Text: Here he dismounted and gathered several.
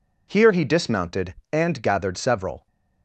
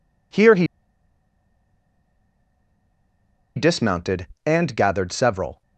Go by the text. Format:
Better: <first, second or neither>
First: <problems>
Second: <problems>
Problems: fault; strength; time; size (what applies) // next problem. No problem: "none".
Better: first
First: none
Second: pauses between "he" and "dismounted"; strong; at 0.6 s; 2.9 s long